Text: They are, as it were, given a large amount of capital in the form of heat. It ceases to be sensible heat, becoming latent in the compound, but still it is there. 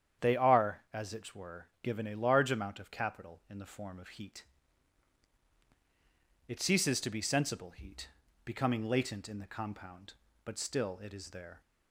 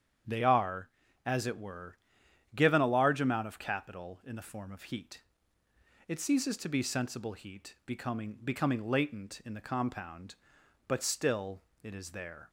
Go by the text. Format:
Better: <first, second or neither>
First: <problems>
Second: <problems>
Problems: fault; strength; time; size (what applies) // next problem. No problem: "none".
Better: first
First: starts louder than the rest; strong; until 1.3 s; 8.5 dB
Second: starts louder than the rest; strong; until 1.6 s; 8 dB // says "becoming" twice; at 8.4 s // pauses between "still" and "it"; slight; at 11.6 s; 0.22 s long